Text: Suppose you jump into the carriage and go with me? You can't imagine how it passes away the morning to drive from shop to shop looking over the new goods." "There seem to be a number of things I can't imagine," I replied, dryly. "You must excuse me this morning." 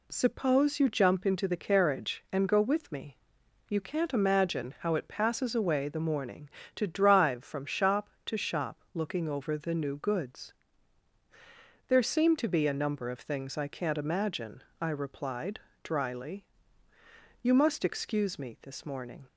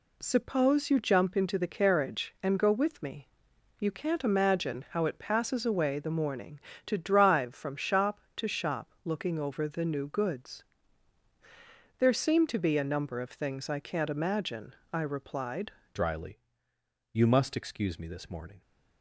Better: first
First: none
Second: changes voice at "dryly"; from 15.9 s on; 2.7 s long

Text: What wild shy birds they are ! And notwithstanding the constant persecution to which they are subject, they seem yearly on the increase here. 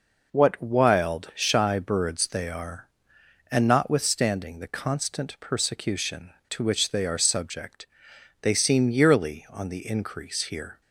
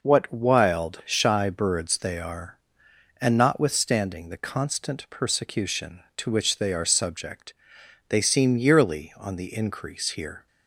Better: neither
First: none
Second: none

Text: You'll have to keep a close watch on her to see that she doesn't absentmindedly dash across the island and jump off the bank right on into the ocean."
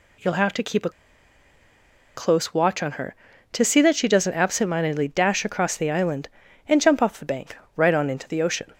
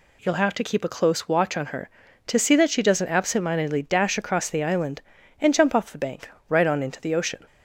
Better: second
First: pauses between "a" and "close"; strong; at 0.8 s; 1.2 s long // pauses between "bank" and "right"; slight; at 7.5 s; 0.18 s long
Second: pauses between "bank" and "right"; slight; at 6.2 s; 0.18 s long

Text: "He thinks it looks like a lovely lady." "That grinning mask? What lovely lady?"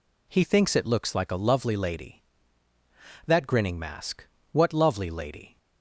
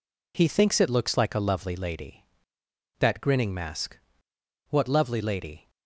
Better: neither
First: none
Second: none

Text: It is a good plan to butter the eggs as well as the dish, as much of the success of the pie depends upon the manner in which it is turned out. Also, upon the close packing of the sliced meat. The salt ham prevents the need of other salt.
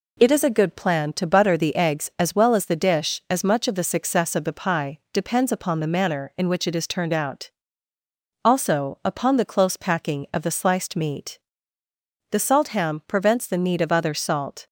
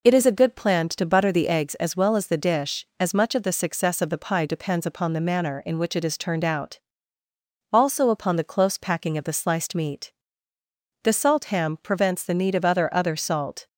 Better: first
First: none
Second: says "other" twice; at 12.9 s

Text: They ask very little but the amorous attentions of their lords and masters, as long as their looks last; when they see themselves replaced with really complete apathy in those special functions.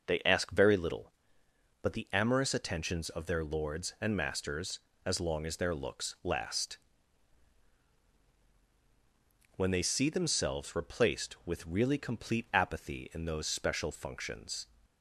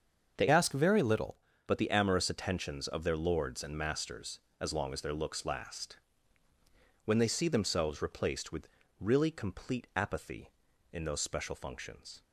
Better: first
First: none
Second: starts louder than the rest; until 1.3 s; 7 dB // changes voice from "ask" to "little"; from 0.4 to 1.3 s; 0.9 s long // pauses between "with" and "really"; slight; at 8.6 s; 0.32 s long

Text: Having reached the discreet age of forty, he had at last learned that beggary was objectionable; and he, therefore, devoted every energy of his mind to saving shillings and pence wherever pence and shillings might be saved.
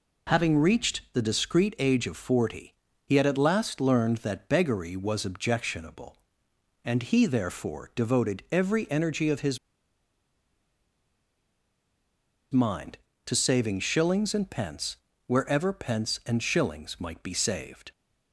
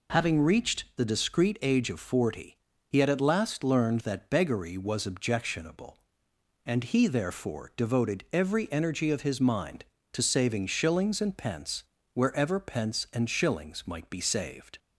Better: second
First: pauses between "his" and "mind"; strong; at 9.5 s; 2.9 s long // pauses between "pence" and "wherever"; slight; at 14.9 s; 0.32 s long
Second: pauses between "pence" and "wherever"; slight; at 11.8 s; 0.32 s long

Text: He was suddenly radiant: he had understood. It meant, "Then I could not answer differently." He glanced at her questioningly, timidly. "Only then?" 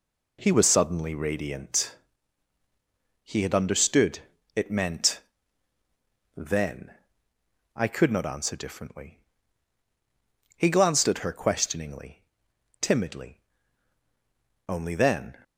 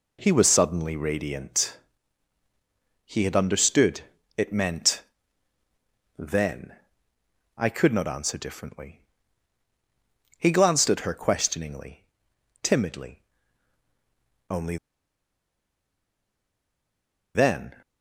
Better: first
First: pauses between "Then" and "I"; noticeable; at 6.9 s; 0.80 s long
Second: pauses between "Then" and "I"; noticeable; at 6.7 s; 0.80 s long // pauses between "Only" and "then"; strong; at 14.7 s; 2.5 s long

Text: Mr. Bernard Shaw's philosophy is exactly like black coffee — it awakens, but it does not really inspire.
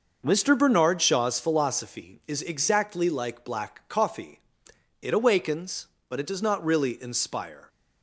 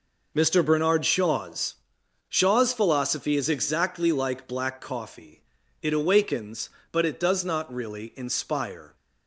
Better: first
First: none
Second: says "Shaw's" twice; at 2.2 s

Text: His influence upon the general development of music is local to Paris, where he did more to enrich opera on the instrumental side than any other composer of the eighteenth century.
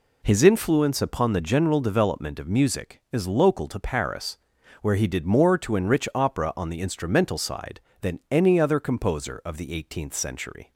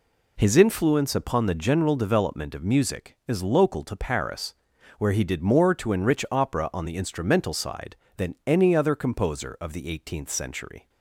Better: neither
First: none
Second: none

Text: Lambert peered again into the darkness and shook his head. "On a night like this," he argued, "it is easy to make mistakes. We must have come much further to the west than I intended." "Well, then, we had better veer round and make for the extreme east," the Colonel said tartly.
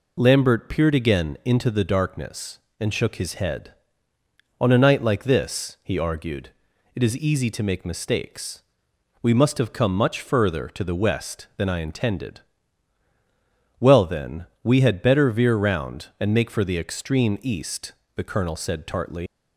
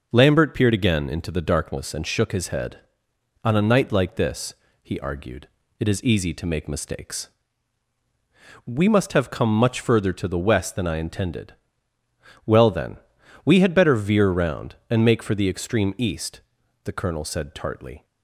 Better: second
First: leaves "tartly" unfinished; at 19.2 s; 115 ms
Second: none

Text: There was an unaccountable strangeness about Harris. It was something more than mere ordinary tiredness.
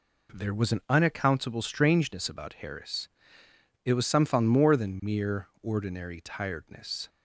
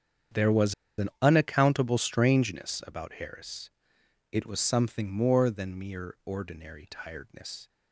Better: first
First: none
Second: starts louder than the rest; strong; until 1.7 s; 8.5 dB // pauses between "was" and "an"; slight; at 0.7 s; 0.24 s long

